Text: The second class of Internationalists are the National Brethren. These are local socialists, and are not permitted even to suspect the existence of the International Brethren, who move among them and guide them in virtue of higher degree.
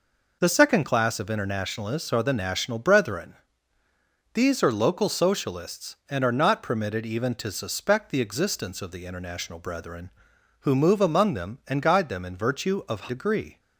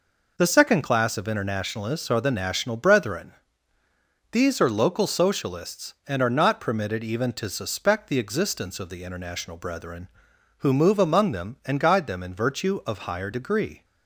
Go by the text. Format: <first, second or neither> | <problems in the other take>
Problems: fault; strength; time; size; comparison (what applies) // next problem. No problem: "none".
second | skips "higher"; at 13.0 s